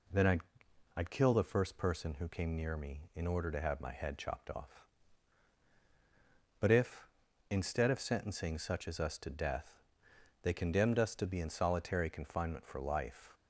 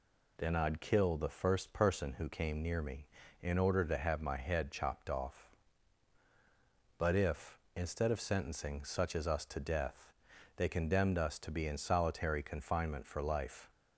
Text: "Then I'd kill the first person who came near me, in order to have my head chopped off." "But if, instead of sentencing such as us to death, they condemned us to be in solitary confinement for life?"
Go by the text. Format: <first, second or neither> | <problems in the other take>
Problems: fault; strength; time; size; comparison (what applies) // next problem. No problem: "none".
second | says "I'd" twice; at 0.9 s